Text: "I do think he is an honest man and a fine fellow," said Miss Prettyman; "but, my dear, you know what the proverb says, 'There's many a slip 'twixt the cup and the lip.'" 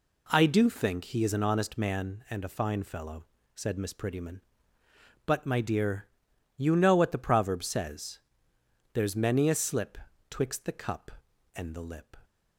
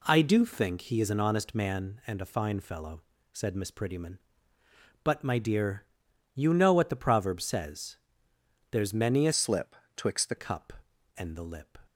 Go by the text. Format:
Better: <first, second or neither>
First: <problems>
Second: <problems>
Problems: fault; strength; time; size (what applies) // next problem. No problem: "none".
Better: first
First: pauses between "slip" and "twixt"; slight; at 9.9 s; 0.32 s long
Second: changes voice from "slip" to "the"; from 9.3 to 10.3 s; 1.0 s long // pauses between "slip" and "twixt"; slight; at 9.7 s; 0.22 s long